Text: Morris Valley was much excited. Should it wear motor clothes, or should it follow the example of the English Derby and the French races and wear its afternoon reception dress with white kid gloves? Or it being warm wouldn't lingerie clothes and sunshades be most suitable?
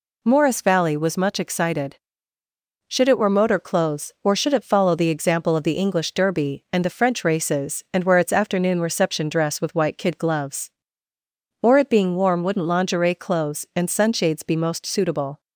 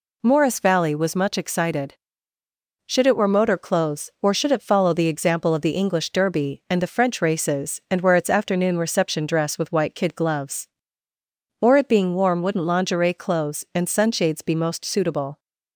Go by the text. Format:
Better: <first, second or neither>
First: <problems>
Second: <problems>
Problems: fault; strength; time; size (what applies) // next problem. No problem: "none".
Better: neither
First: none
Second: none